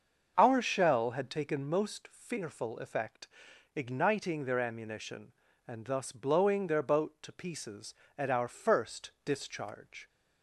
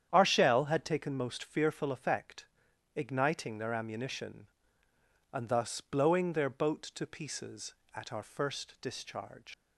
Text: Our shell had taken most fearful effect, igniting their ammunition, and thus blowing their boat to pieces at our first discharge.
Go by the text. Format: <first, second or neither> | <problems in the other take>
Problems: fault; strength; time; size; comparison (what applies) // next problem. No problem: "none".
first | starts louder than the rest; strong; until 1.1 s; 9 dB; also in the first // leaves "discharge" unfinished; at 9.5 s; 95 ms